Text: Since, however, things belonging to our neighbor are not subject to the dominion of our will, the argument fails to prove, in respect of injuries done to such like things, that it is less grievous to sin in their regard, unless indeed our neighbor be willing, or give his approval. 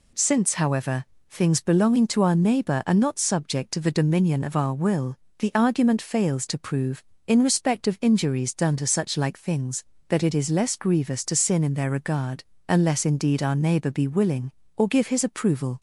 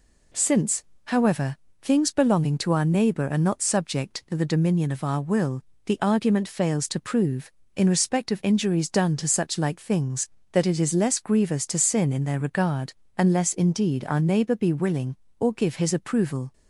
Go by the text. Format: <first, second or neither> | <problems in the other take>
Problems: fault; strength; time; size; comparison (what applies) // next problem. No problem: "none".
neither | none